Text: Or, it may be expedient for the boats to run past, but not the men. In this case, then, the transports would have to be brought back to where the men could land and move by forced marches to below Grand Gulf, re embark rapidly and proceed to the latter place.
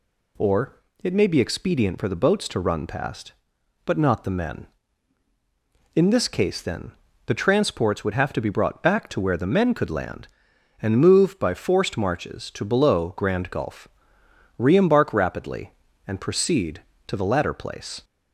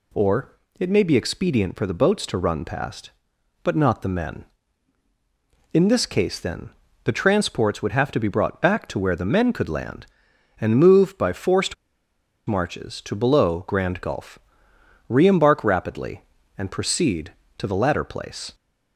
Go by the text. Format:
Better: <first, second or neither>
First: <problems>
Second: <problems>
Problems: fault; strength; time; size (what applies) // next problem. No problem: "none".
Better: first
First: none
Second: pauses between "forced" and "marches"; noticeable; at 11.7 s; 0.72 s long